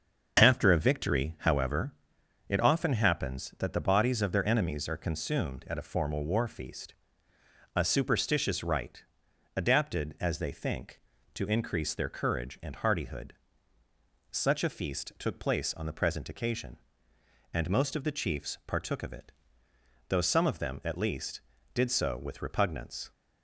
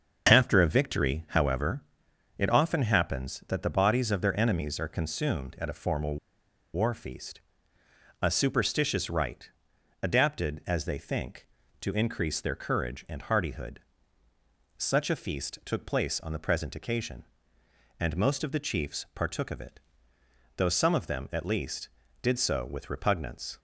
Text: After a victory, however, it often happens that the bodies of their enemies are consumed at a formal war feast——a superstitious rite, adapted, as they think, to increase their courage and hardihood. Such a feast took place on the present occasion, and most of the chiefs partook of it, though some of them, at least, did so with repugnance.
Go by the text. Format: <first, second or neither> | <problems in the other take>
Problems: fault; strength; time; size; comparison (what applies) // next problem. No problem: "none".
first | starts louder than the rest; until 1.3 s; 6.5 dB; also in the first // pauses between "formal" and "war"; noticeable; at 6.1 s; 0.56 s long